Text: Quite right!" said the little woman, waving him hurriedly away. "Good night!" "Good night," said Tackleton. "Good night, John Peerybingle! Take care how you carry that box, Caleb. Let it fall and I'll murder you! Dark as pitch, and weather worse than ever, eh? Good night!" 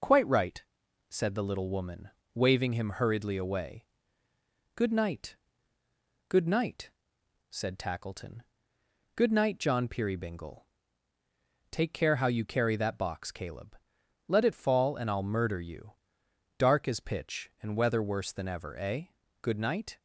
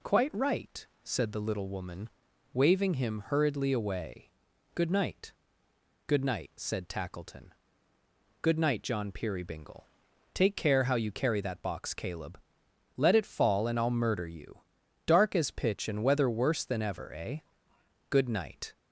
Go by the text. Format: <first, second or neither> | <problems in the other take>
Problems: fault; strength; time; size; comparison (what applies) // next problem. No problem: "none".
neither | none